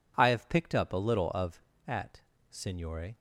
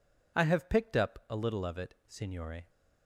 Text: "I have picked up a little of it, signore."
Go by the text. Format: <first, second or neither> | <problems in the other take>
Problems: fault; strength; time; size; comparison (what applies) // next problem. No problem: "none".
second | says "at" for "it"; at 1.8 s